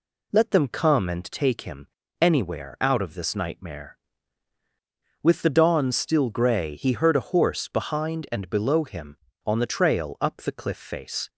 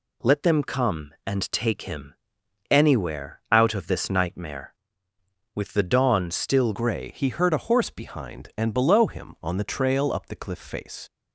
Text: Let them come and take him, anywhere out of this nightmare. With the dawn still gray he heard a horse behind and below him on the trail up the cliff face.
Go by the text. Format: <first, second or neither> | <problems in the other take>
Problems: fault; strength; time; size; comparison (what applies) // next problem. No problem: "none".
first | changes voice at "gray"; from 6.7 s on; 4.3 s long